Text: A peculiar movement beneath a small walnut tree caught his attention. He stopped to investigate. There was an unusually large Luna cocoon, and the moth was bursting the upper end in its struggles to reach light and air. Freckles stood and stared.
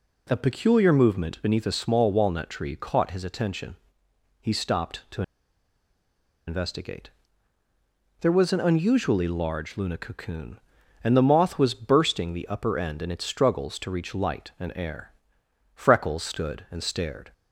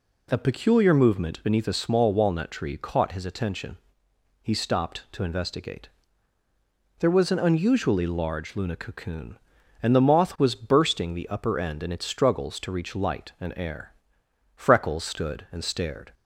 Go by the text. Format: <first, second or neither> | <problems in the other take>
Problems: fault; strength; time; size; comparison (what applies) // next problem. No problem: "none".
second | pauses between "to" and "investigate"; strong; at 5.2 s; 1.2 s long